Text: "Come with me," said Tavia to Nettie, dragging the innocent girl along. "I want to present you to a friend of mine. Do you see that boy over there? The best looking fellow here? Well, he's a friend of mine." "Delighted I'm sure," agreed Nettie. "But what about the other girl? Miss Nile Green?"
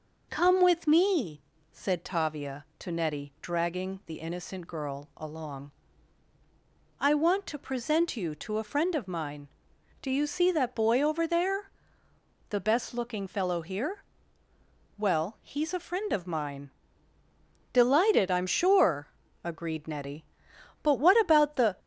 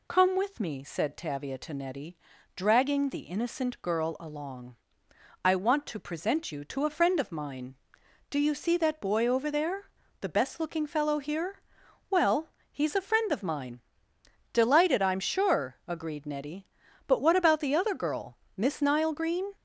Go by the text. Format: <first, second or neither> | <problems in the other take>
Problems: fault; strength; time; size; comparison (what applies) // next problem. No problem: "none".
second | stops before "other girl Miss Nile Green"; at 21.7 s